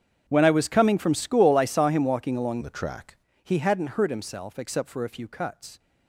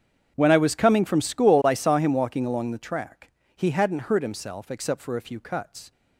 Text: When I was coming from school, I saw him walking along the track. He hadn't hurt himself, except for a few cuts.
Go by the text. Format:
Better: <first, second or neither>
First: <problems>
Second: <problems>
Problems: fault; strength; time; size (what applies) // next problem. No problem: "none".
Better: second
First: starts louder than the rest; strong; until 1.2 s; 8 dB // changes voice from "the" to "track"; from 2.6 to 3.1 s; 0.5 s long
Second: starts louder than the rest; strong; until 1.3 s; 8 dB